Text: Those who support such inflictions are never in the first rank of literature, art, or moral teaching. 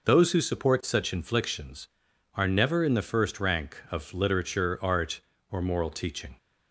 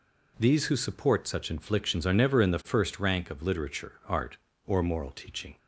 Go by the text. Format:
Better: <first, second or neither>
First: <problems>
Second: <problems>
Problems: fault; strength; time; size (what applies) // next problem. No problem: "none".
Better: first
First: none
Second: says "These" for "Those"; at 0.3 s